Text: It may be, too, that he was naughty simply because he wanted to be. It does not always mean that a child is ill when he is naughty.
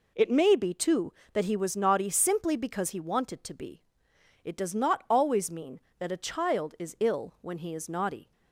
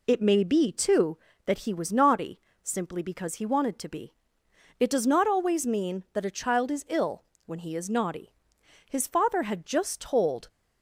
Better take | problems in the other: first | pauses between "naughty" and "simply"; slight; at 2.4 s; 0.22 s long // pauses between "ill" and "when"; slight; at 7.2 s; 0.24 s long // goes on to say "His father had just told"; from 8.9 s on; 1.5 s long

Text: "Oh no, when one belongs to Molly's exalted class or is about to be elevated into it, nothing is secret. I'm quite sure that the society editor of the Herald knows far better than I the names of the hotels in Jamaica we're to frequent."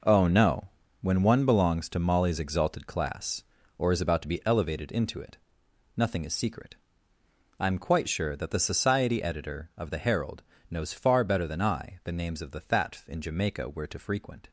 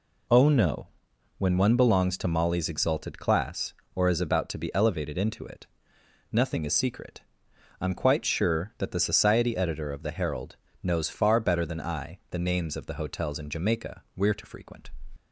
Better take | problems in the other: second | pauses between "Herald" and "knows"; slight; at 10.4 s; 0.26 s long; slight in the second // says "thatf" for "hotels"; at 12.6 s

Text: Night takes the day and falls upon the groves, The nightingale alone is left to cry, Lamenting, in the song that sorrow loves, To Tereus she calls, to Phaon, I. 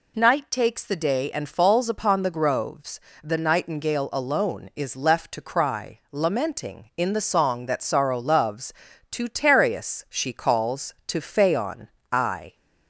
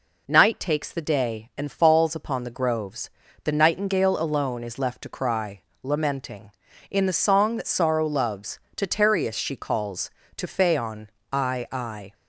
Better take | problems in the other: first | says "I" twice; at 11.7 s

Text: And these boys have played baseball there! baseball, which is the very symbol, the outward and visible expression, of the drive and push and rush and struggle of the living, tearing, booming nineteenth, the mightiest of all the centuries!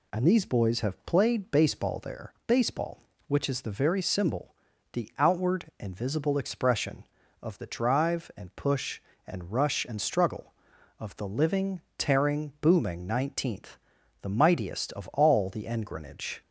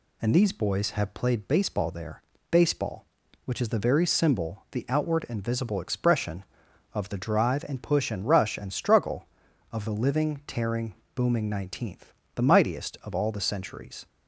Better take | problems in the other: second | says "engrenage" for "centuries"; at 15.6 s

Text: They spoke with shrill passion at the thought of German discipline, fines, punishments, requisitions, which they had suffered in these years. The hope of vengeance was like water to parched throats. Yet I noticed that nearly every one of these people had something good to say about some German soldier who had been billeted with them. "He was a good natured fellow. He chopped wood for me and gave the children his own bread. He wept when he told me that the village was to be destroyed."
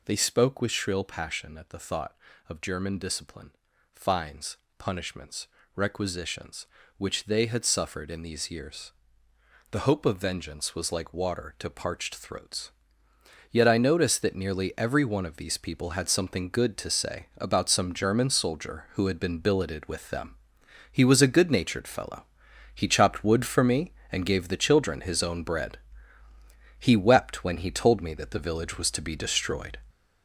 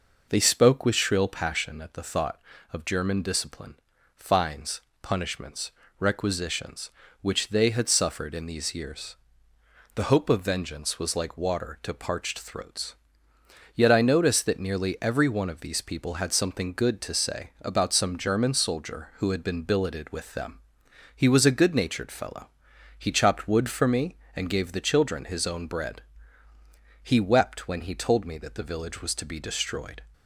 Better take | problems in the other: second | gets louder; noticeable; throughout; 6 dB

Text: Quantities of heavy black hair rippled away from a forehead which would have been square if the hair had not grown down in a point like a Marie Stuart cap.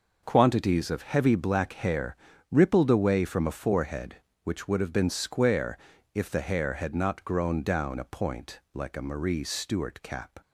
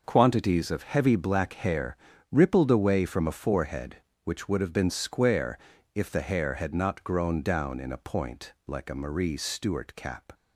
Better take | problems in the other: second | pauses between "hair" and "rippled"; slight; at 2.1 s; 0.34 s long; slight in the second // pauses between "square" and "if"; at 5.7 s; 0.38 s long; also in the second // skips "in"; at 7.9 s // pauses between "point" and "like"; slight; at 8.5 s; 0.16 s long; slight in the second

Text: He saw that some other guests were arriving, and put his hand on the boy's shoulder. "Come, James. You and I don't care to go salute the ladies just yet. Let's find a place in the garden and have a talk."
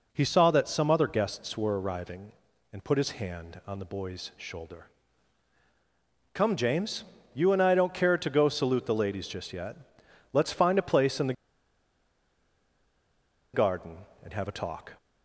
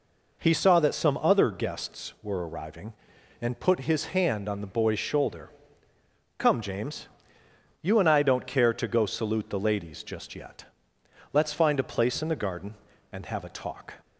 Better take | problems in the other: second | pauses between "the" and "garden"; strong; at 11.3 s; 2.1 s long

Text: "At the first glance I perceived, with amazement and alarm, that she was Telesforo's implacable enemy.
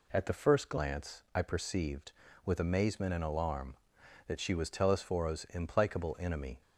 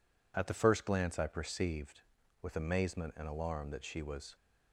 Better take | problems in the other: first | stops before "Telesforo's implacable enemy"; at 4.3 s

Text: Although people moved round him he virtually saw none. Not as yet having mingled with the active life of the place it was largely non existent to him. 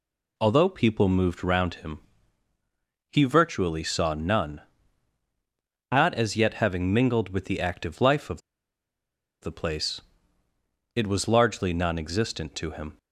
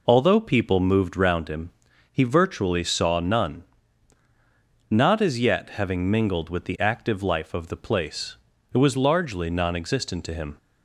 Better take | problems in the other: second | pauses between "him" and "he"; at 2.0 s; 1.1 s long; also in the second // pauses between "of" and "the"; at 8.4 s; 1.0 s long // pauses between "place" and "it"; noticeable; at 10.0 s; 0.94 s long; slight in the second

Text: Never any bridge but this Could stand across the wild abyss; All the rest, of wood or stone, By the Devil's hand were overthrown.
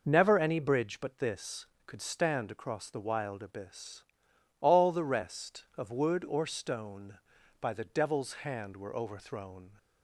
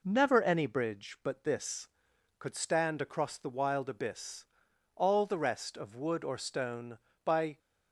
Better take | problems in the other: first | stops before "the Devil's hand were overthrown"; at 7.5 s

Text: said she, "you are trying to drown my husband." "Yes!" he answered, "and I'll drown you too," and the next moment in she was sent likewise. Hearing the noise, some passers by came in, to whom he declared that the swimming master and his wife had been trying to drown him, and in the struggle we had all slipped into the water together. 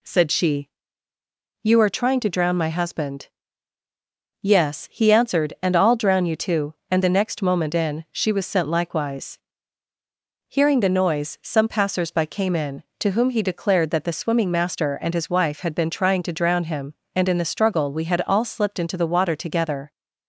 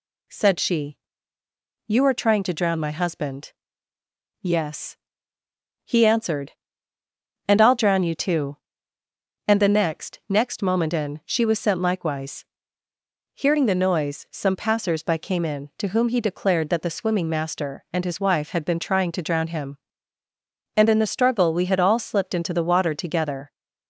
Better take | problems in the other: first | says "next" twice; at 10.2 s

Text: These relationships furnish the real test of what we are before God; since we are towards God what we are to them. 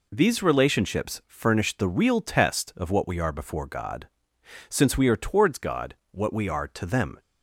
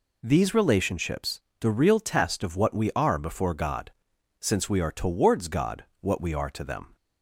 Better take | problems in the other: first | skips "furnish"; at 1.5 s // pauses between "God" and "what"; slight; at 5.8 s; 0.16 s long; slight in the first

